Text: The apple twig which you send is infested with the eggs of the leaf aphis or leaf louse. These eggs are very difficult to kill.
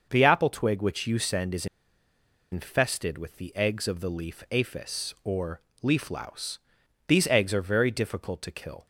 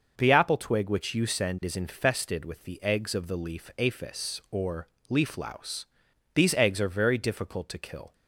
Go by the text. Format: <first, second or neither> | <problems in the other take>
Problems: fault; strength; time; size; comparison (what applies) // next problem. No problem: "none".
second | starts louder than the rest; noticeable; until 1.1 s; 6 dB; noticeable in the second // pauses between "is" and "infested"; noticeable; at 1.6 s; 0.85 s long // pauses between "or" and "leaf"; slight; at 5.5 s; 0.24 s long; slight in the second